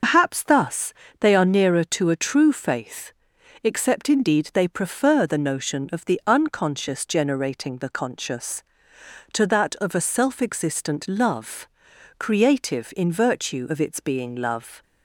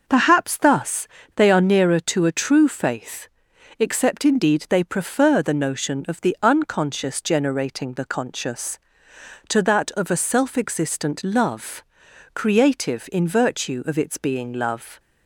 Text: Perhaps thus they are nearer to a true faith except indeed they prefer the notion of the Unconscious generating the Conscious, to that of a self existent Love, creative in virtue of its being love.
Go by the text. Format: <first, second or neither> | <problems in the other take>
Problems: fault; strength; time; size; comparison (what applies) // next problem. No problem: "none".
second | loses the start of "Perhaps"; at 0.0 s; 95 ms // pauses between "thus" and "they"; slight; at 0.9 s; 0.28 s long; slight in the second // pauses between "faith" and "except"; noticeable; at 3.1 s; 0.54 s long; noticeable in the second